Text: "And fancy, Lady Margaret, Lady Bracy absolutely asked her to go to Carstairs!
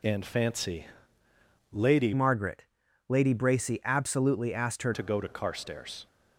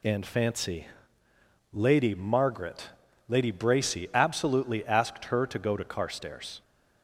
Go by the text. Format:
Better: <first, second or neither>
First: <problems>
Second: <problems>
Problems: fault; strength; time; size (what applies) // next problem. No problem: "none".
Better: second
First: changes voice from "Margaret" to "her"; from 2.1 to 4.9 s; 2.8 s long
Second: none